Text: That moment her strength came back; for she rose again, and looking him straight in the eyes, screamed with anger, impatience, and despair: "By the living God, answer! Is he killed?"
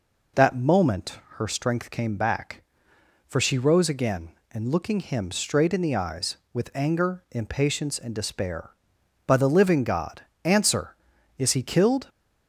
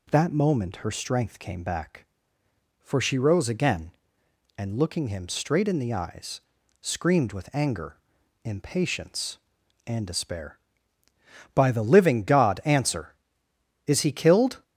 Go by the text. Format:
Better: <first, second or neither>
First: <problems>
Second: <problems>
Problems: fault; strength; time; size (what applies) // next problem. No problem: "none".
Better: second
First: pauses between "moment" and "her"; slight; at 1.1 s; 0.18 s long // skips "screamed"; at 6.4 s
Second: none